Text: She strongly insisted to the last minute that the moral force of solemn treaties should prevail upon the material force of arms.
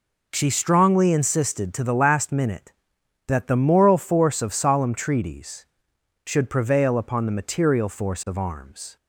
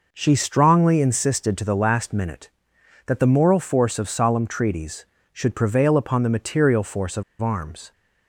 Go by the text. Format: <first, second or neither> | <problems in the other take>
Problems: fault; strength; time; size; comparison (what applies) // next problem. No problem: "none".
first | pauses between "of" and "arms"; slight; at 7.2 s; 0.18 s long